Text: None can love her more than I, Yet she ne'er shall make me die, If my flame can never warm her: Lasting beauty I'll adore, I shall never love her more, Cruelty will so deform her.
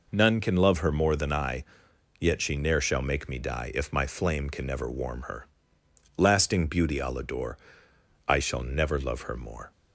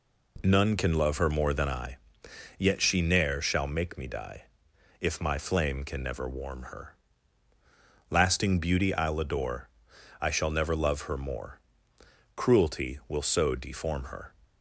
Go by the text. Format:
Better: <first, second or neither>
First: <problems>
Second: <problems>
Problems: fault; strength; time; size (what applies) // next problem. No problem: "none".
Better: second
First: stops before "Cruelty will so deform her"; at 9.7 s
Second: none